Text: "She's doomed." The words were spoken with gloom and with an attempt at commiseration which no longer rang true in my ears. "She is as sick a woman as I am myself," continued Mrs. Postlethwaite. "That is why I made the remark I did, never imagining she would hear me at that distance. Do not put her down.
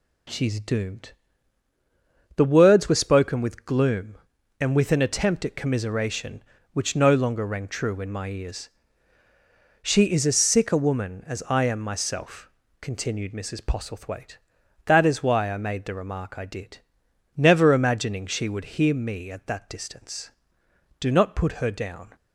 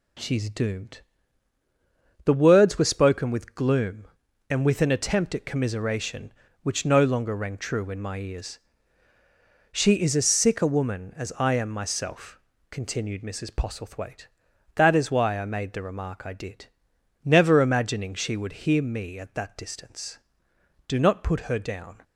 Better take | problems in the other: neither | none

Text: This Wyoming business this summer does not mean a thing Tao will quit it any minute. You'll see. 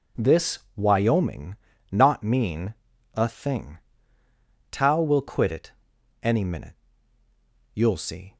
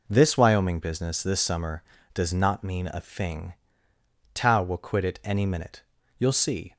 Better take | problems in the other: second | pauses between "This" and "Wyoming"; slight; at 0.6 s; 0.16 s long // skips "business this summer does"; at 1.7 s // pauses between "mean" and "a"; at 2.7 s; 0.40 s long // pauses between "thing" and "Tao"; noticeable; at 3.7 s; 0.94 s long; noticeable in the second // pauses between "it" and "any"; noticeable; at 5.7 s; 0.50 s long

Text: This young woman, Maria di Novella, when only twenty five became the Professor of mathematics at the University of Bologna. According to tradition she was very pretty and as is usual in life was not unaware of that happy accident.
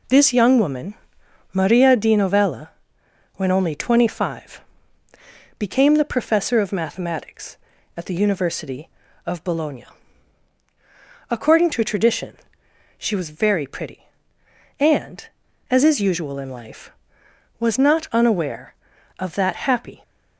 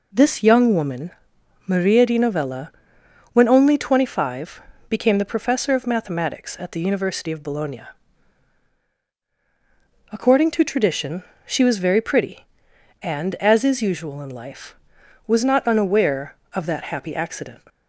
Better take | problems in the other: second | pauses between "five" and "became"; noticeable; at 4.6 s; 0.96 s long; slight in the second // pauses between "tradition" and "she"; noticeable; at 12.3 s; 0.62 s long; slight in the second // stops before "accident"; at 20.0 s

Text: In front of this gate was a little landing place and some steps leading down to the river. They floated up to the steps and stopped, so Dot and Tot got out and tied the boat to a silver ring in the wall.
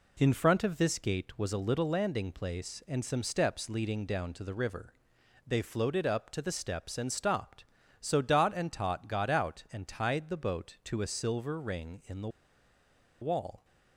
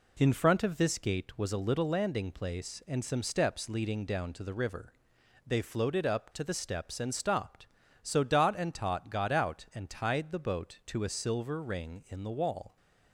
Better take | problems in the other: second | pauses between "the" and "wall"; noticeable; at 12.2 s; 0.93 s long

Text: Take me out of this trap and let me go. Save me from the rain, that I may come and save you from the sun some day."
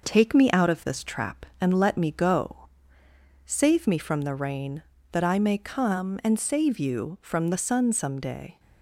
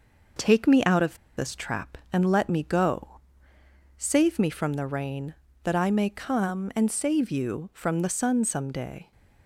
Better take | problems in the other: first | pauses between "of" and "this"; slight; at 1.1 s; 0.22 s long

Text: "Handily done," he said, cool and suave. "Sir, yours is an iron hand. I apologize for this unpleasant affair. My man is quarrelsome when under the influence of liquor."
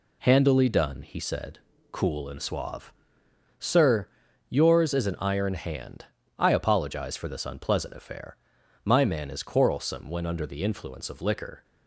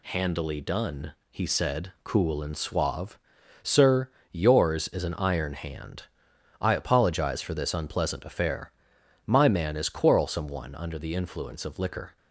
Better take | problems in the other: first | says "one" for "when"; at 10.4 s

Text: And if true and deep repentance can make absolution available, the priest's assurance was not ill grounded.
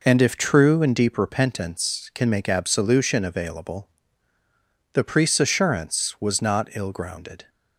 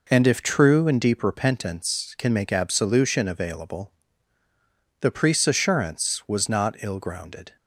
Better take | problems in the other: neither | none

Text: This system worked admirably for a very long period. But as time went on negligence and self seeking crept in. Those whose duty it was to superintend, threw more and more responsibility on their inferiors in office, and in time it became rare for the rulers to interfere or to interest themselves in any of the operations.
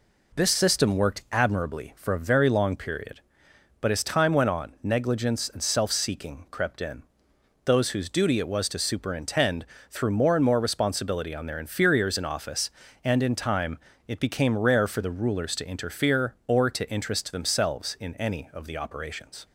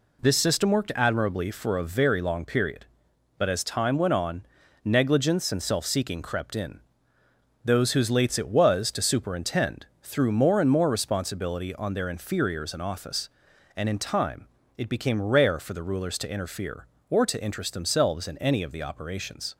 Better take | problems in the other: first | pauses between "on" and "negligence"; at 4.4 s; 0.40 s long // says "lates" for "duty"; at 8.0 s // pauses between "time" and "it"; slight; at 14.4 s; 0.32 s long; slight in the first

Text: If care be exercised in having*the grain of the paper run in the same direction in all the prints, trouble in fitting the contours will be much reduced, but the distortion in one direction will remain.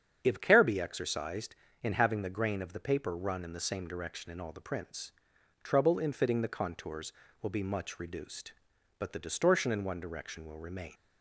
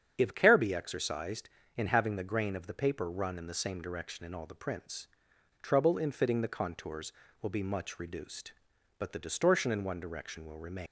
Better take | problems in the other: first | starts louder than the rest; strong; until 1.1 s; 8 dB; strong in the first // leaves "remain" unfinished; at 10.8 s; 70 ms

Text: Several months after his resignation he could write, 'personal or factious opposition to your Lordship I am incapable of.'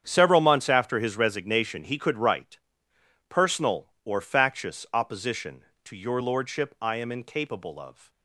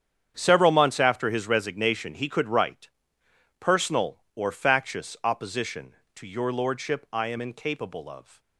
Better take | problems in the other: neither | starts louder than the rest; strong; the same in both

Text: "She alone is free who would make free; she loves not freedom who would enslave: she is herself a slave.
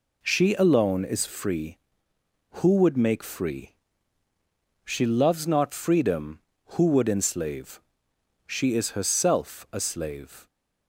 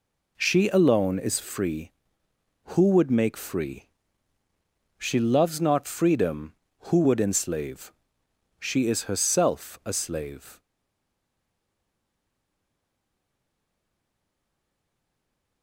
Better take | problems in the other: first | stays silent after the last word; strong; from 10.5 s on; 5.1 s long

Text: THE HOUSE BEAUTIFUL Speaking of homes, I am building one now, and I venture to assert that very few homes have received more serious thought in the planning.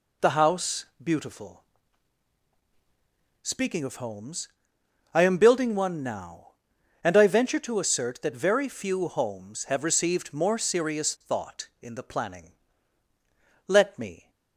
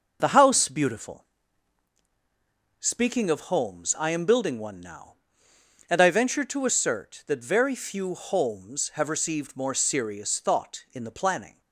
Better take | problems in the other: second | pauses between "HOUSE" and "BEAUTIFUL"; slight; at 0.8 s; 0.18 s long // pauses between "BEAUTIFUL" and "Speaking"; strong; at 1.6 s; 1.8 s long; strong in the second // goes on to say "Let me"; noticeable; from 13.6 s on; 0.64 s long

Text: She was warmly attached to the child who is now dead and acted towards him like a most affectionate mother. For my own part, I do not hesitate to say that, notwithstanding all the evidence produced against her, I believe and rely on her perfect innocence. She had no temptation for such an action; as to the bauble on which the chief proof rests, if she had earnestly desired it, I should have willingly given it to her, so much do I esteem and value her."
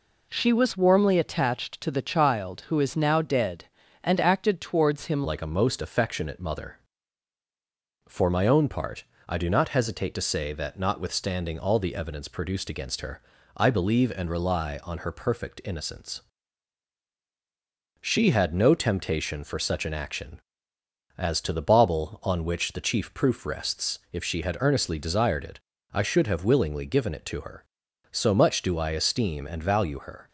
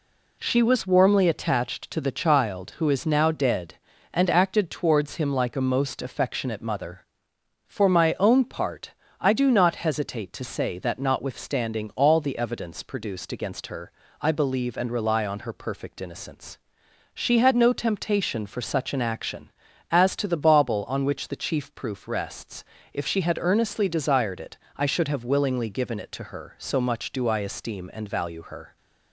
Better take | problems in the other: second | changes voice at "like"; from 5.2 s on; 25.0 s long

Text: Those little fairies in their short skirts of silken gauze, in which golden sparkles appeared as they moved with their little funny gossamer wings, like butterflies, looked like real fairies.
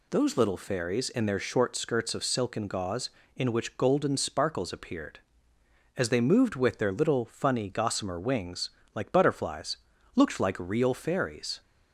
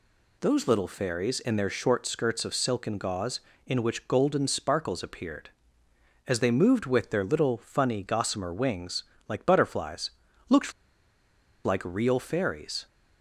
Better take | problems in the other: first | pauses between "looked" and "like"; noticeable; at 10.7 s; 0.92 s long

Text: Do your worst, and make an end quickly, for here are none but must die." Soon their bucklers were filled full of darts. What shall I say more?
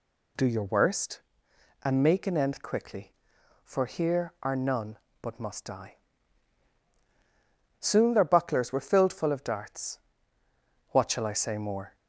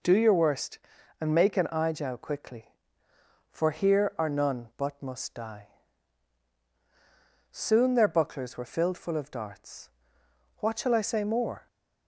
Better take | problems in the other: first | says "ijow" for "end"; at 1.7 s

